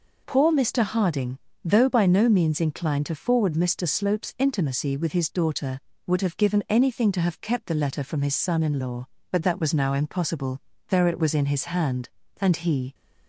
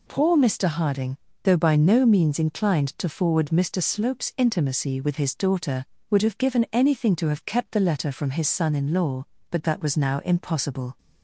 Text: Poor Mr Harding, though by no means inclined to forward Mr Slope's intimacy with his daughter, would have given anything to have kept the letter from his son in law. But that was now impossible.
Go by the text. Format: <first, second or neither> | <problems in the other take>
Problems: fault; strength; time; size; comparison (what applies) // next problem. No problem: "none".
second | goes on to say "There it was in his hand and he"; strong; from 10.8 s on; 2.0 s long